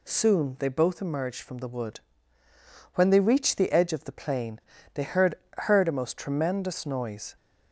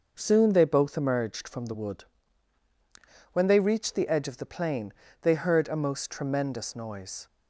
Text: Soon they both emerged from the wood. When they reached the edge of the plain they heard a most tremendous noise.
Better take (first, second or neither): second